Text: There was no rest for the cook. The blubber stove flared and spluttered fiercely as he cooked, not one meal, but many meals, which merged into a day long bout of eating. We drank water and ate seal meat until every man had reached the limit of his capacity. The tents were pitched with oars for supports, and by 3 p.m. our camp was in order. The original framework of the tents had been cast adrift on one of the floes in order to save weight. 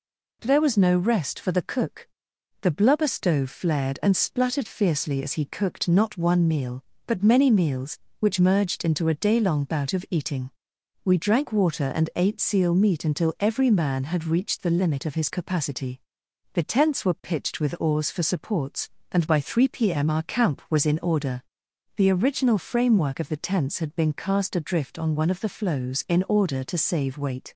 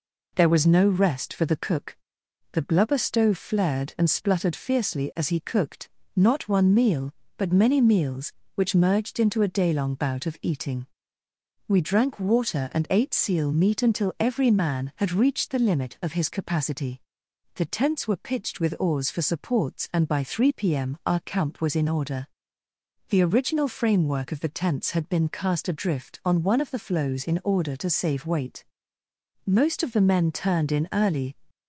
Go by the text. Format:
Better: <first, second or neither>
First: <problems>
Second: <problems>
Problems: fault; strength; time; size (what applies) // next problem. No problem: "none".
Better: first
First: none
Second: goes on to say "Most of the men turned in early"; strong; from 29.4 s on; 1.8 s long